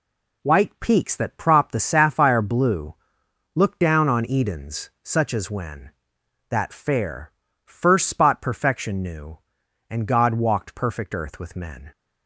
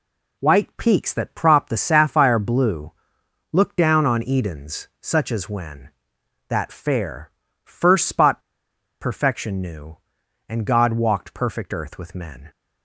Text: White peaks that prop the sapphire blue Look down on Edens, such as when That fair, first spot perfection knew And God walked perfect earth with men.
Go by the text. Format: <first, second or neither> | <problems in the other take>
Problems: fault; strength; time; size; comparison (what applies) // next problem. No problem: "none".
first | pauses between "blue" and "Look"; noticeable; at 2.9 s; 0.60 s long; noticeable in the first // pauses between "spot" and "perfection"; noticeable; at 8.3 s; 0.62 s long